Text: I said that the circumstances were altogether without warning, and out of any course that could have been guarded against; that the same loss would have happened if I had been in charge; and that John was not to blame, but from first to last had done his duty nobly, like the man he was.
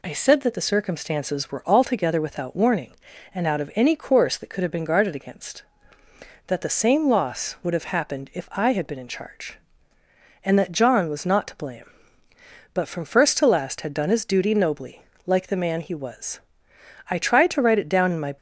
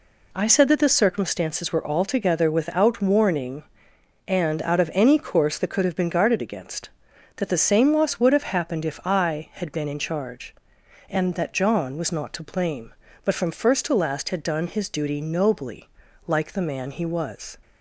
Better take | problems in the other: second | goes on to say "I tried to write it down in my"; noticeable; from 17.1 s on; 1.2 s long

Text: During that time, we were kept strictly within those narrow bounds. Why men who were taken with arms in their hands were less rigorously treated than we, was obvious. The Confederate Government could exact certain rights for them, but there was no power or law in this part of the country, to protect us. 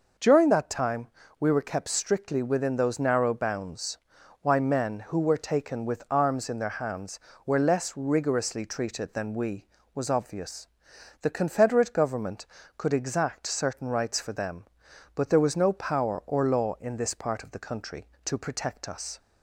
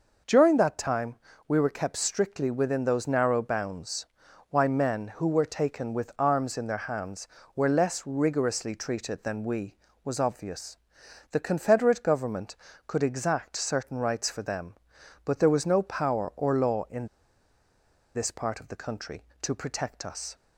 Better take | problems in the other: first | pauses between "in" and "this"; at 17.0 s; 1.0 s long

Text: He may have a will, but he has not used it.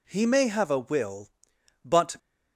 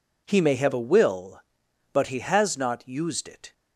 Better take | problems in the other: second | stops before "he has not used it"; at 2.1 s

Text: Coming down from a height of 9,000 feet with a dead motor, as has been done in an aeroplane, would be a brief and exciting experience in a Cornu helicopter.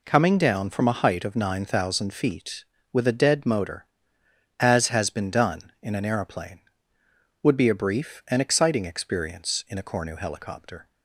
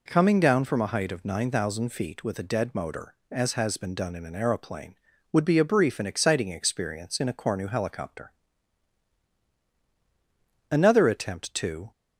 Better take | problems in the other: first | goes on to say "Another attempt to"; noticeable; from 10.7 s on; 1.2 s long

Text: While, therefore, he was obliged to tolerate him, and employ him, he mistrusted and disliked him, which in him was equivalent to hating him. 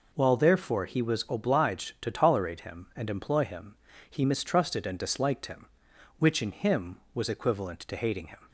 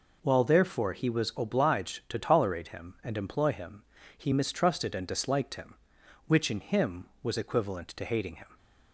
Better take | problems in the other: neither | none

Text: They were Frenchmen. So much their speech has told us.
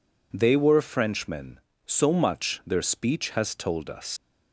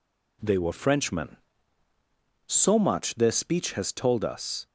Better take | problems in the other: second | leaves "us" unfinished; at 4.1 s; 100 ms

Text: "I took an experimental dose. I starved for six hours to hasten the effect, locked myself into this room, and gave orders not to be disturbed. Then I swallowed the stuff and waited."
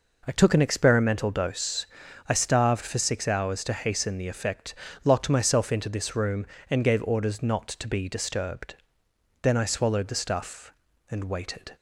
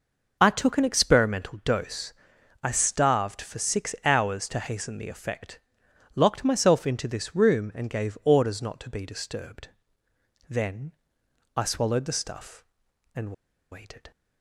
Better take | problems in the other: first | pauses between "Then" and "I"; noticeable; at 10.9 s; 0.64 s long // pauses between "and" and "waited"; at 13.3 s; 0.39 s long

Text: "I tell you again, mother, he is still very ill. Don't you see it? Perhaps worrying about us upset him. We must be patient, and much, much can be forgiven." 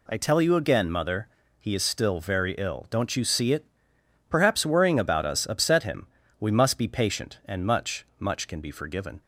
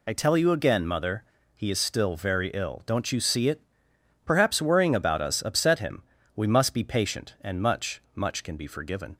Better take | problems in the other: first | loses the start of "I"; at 0.0 s; 35 ms

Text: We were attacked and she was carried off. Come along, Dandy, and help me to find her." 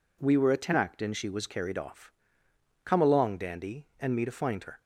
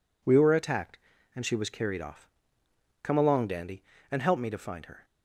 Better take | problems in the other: second | skips "help"; at 4.1 s

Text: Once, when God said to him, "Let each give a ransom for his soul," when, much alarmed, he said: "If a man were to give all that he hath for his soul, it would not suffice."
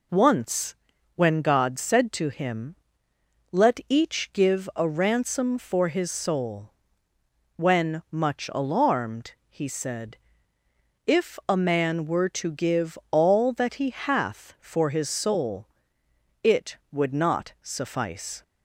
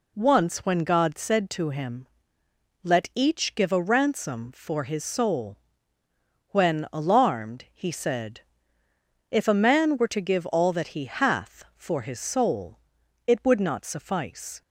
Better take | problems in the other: first | skips "much"; at 6.8 s

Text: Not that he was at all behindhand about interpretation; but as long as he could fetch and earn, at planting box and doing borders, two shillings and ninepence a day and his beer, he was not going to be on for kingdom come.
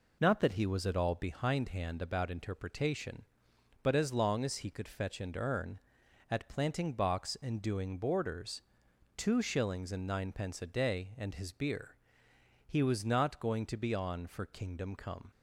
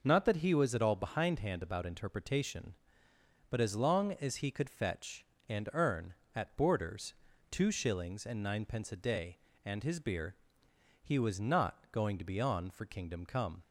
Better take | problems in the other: first | skips "planting box and doing"; at 6.5 s

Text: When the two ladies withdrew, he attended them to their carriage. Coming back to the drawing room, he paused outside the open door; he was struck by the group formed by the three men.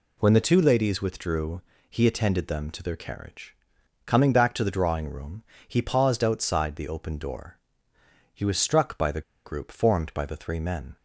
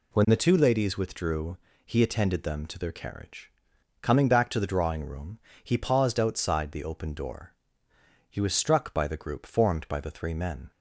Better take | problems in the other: second | pauses between "the" and "group"; slight; at 9.2 s; 0.24 s long

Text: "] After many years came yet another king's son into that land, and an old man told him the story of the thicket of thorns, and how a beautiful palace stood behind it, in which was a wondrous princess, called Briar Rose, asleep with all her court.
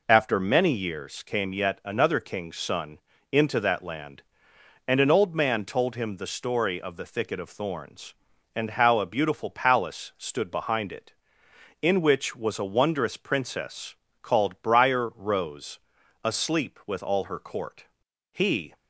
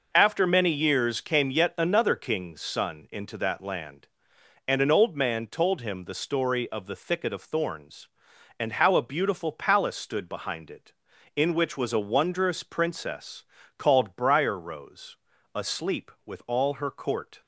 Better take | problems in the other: second | pauses between "son" and "into"; slight; at 2.9 s; 0.32 s long // goes on to say "He"; slight; from 18.3 s on; 0.44 s long

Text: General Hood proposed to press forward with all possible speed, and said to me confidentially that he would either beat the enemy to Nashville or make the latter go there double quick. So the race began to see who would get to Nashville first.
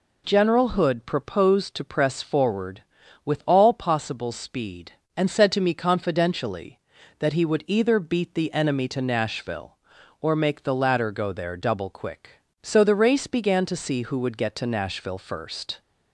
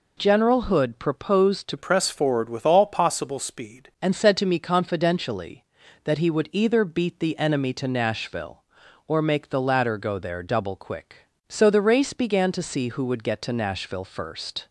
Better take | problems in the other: first | changes voice from "press" to "speed"; from 1.7 to 3.8 s; 2.1 s long

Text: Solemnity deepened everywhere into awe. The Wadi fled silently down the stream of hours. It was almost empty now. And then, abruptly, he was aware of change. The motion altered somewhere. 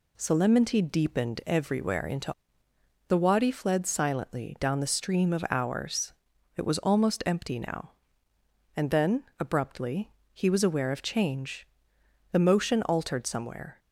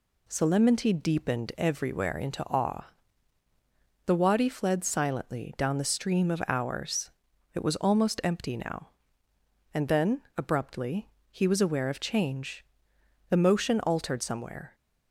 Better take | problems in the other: second | skips "awe"; at 2.7 s

